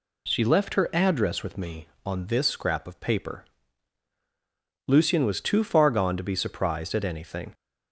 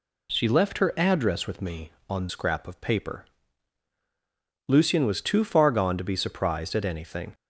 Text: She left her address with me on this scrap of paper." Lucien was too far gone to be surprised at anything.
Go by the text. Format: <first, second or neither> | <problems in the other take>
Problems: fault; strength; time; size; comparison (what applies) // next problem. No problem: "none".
first | skips "this"; at 2.2 s